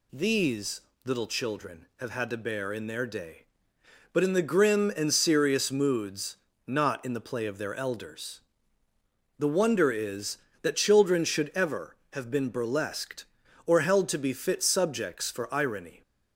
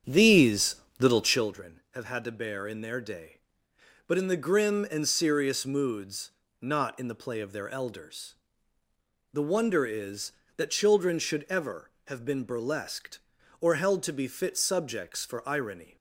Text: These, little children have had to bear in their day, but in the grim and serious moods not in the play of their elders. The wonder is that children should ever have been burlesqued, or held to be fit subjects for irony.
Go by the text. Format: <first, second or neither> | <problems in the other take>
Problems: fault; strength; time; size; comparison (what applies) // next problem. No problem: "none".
first | starts louder than the rest; strong; until 1.6 s; 8 dB // pauses between "moods" and "not"; slight; at 6.2 s; 0.30 s long; slight in the first